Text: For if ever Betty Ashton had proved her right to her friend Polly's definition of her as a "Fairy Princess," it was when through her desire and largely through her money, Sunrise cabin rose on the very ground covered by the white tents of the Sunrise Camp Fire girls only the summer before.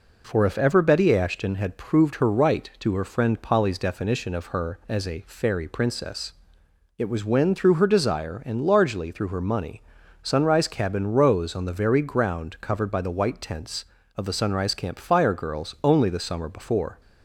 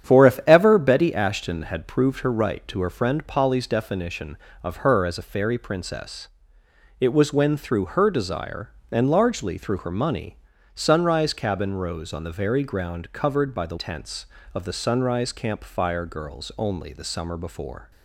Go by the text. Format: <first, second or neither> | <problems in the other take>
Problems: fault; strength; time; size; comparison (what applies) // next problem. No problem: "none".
first | starts louder than the rest; strong; until 1.1 s; 9 dB // skips "white"; at 13.7 s